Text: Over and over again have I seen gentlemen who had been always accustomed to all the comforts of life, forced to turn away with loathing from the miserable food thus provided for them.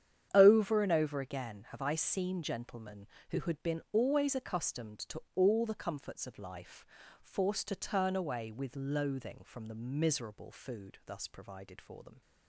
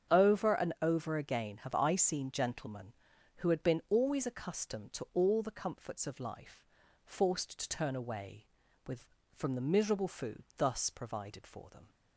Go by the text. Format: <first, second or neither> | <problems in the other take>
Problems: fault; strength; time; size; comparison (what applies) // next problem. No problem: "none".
first | starts louder than the rest; strong; until 1.2 s; 7.5 dB; strong in the first // skips "loathing"; at 9.2 s